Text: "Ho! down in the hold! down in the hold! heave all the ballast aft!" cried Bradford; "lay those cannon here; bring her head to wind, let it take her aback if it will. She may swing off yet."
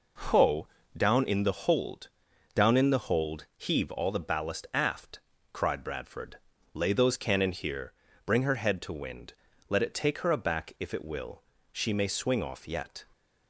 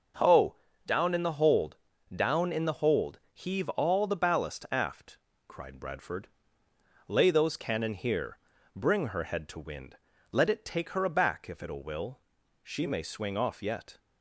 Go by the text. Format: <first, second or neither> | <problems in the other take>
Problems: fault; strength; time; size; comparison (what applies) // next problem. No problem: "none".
first | starts louder than the rest; until 1.5 s; 6.5 dB // says "will" twice; at 11.8 s